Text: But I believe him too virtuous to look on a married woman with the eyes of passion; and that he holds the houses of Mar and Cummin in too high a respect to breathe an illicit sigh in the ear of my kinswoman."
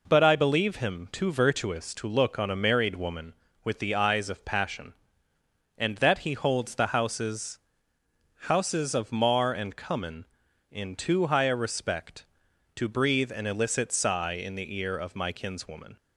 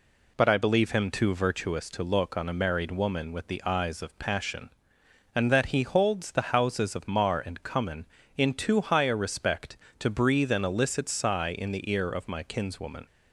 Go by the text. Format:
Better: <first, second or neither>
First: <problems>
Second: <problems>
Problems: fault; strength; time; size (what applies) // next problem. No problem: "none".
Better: second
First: says "houses" twice; at 8.4 s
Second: none